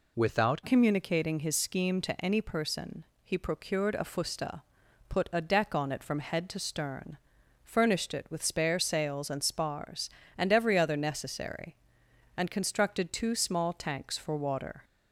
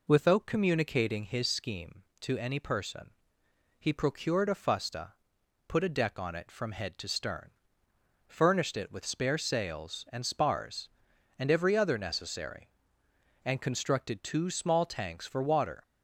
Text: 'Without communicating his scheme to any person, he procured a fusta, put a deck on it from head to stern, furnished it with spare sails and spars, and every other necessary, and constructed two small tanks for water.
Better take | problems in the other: second | changes voice at "communicating"; from 0.6 s on; 14.2 s long

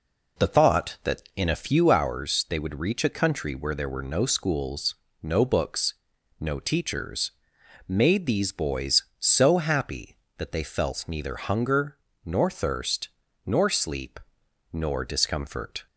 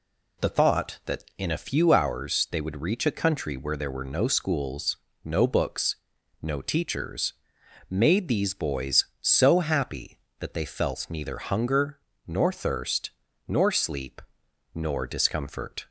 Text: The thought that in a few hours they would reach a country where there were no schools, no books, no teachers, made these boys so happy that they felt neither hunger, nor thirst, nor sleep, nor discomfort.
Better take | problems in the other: second | starts louder than the rest; noticeable; until 1.9 s; 4 dB

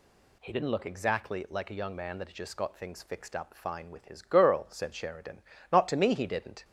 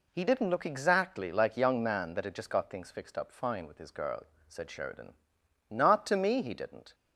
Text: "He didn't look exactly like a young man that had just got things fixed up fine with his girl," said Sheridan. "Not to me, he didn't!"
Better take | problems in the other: first | skips "a"; at 1.5 s

